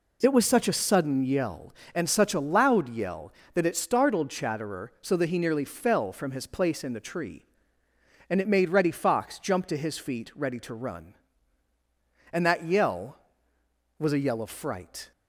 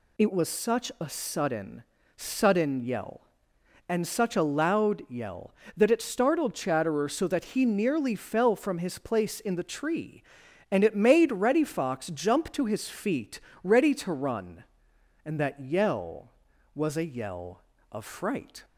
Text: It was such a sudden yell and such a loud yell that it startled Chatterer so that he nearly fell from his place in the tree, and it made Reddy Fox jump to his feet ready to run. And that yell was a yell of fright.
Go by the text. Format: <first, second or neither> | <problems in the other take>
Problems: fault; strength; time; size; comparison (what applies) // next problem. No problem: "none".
first | says "sudden" twice; at 2.1 s // pauses between "feet" and "ready"; slight; at 13.4 s; 0.22 s long